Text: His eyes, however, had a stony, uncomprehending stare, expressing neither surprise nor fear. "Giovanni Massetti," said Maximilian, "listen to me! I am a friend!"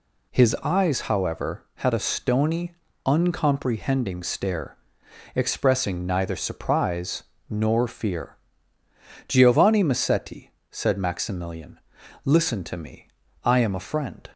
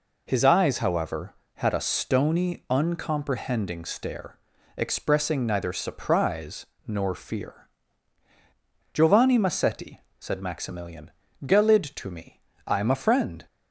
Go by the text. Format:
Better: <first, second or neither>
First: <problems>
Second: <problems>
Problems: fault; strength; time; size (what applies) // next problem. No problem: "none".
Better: first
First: pauses between "surprise" and "nor"; slight; at 7.2 s; 0.26 s long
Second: pauses between "surprise" and "nor"; slight; at 6.6 s; 0.20 s long // says "gelid" for "listen"; at 11.4 s